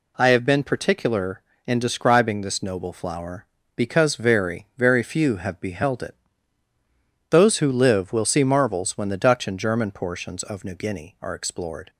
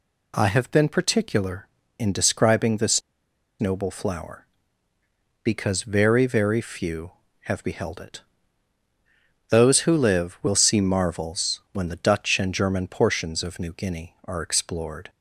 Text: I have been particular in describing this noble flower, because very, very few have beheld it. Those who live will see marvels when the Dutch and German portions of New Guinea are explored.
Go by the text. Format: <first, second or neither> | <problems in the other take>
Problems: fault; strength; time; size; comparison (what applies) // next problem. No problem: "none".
first | pauses between "this" and "noble"; noticeable; at 3.0 s; 0.58 s long